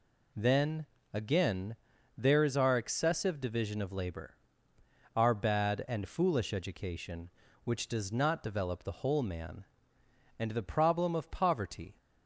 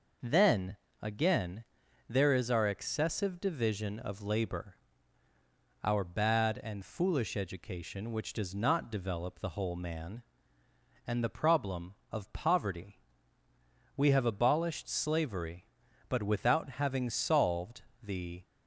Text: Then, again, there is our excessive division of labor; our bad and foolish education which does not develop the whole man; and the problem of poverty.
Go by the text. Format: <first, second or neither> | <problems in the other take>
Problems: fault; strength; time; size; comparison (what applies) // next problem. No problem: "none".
first | goes on to say "We have abolished slavery but without having solved the"; strong; from 13.9 s on; 4.4 s long